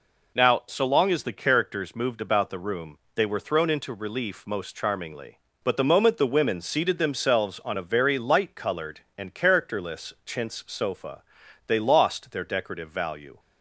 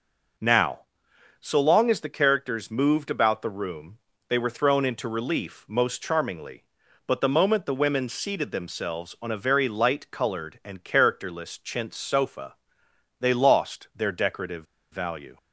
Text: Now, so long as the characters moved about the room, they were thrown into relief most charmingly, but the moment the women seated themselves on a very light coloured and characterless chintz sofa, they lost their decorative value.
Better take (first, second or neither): first